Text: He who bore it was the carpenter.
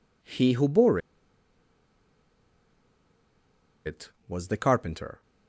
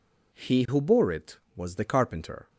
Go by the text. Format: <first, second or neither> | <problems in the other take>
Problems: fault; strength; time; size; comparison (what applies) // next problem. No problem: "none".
second | pauses between "bore" and "it"; strong; at 0.9 s; 2.8 s long